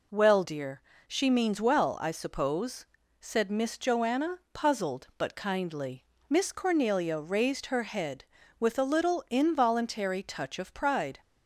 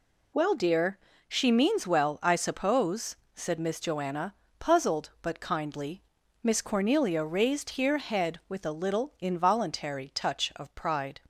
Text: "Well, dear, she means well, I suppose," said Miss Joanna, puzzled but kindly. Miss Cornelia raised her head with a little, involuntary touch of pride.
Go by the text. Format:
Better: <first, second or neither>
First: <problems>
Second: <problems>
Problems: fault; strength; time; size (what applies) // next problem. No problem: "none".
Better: first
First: none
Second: says "here" for "her"; at 7.6 s